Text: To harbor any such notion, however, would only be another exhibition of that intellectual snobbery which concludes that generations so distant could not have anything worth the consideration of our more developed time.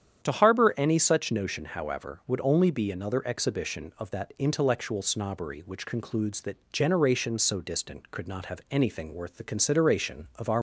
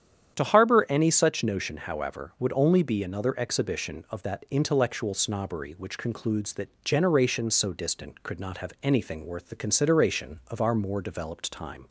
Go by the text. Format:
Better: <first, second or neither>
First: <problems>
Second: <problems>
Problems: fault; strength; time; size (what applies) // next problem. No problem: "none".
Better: second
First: starts louder than the rest; strong; until 1.2 s; 9 dB // pauses between "that" and "generations"; slight; at 6.5 s; 0.16 s long // stops before "more developed time"; at 10.5 s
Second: starts louder than the rest; strong; until 1.3 s; 9 dB // pauses between "that" and "generations"; slight; at 6.6 s; 0.16 s long